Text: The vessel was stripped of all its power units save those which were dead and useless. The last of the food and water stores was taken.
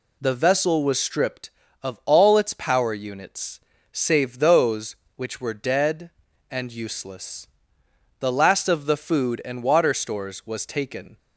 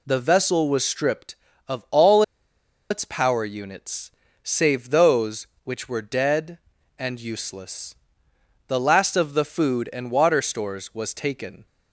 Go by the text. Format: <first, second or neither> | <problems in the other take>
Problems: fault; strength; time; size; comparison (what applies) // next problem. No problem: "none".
first | pauses between "all" and "its"; noticeable; at 2.2 s; 0.68 s long // pauses between "units" and "save"; slight; at 4.1 s; 0.32 s long; slight in the first